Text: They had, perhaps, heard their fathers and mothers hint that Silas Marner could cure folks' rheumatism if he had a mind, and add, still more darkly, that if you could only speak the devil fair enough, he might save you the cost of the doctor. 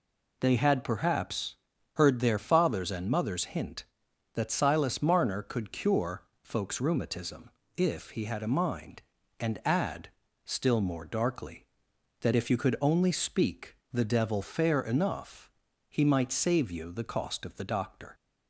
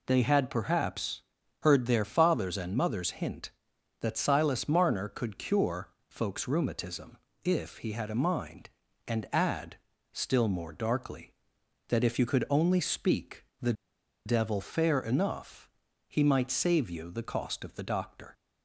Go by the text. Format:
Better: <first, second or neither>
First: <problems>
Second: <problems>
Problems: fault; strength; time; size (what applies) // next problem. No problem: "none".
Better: first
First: pauses between "cure" and "folks"; slight; at 6.2 s; 0.20 s long // pauses between "rheumatism" and "if"; slight; at 7.4 s; 0.26 s long // pauses between "speak" and "the"; slight; at 13.7 s; 0.16 s long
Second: pauses between "cure" and "folks"; slight; at 5.8 s; 0.20 s long // pauses between "rheumatism" and "if"; slight; at 7.1 s; 0.26 s long // pauses between "speak" and "the"; slight; at 13.4 s; 0.16 s long // pauses between "the" and "devil"; noticeable; at 13.7 s; 0.52 s long